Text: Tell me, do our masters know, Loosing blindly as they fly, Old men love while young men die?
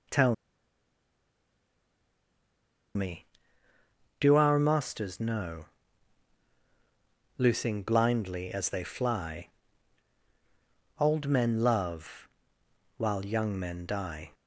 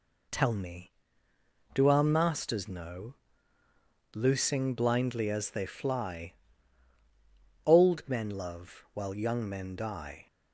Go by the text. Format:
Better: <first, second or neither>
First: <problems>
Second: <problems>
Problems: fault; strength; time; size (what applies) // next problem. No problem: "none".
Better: second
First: starts louder than the rest; noticeable; until 4.6 s; 6 dB // pauses between "Tell" and "me"; strong; at 0.3 s; 2.6 s long // pauses between "love" and "while"; noticeable; at 12.2 s; 0.70 s long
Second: none